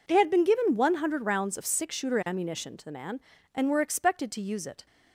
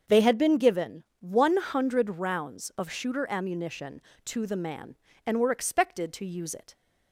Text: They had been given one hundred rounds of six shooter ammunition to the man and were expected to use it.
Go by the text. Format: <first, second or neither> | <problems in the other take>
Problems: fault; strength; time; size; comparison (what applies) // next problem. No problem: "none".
first | starts louder than the rest; until 1.2 s; 7 dB // pauses between "given" and "one"; slight; at 1.0 s; 0.16 s long // skips "six"; at 2.8 s